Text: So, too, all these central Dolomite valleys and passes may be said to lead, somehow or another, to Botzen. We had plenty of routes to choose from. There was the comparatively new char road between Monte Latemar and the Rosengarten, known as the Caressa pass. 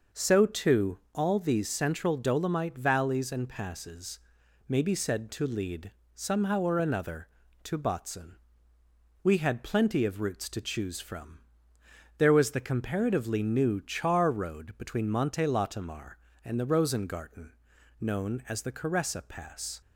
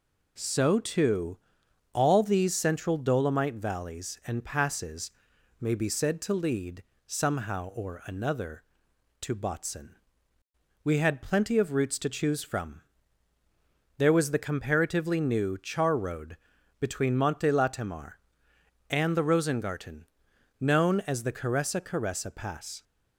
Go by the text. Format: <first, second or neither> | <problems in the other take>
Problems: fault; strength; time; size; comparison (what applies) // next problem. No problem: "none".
first | pauses between "passes" and "may"; noticeable; at 5.0 s; 0.52 s long; noticeable in the first // pauses between "road" and "between"; noticeable; at 16.3 s; 0.46 s long // says "Caressa" twice; at 21.7 s